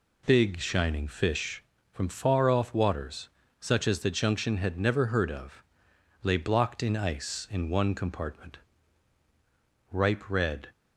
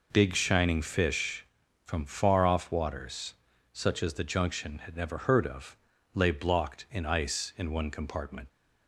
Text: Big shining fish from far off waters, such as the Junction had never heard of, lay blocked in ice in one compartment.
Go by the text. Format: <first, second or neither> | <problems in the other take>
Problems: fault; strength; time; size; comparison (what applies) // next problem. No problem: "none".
second | goes on to say "Ripe red"; noticeable; from 9.9 s on; 0.76 s long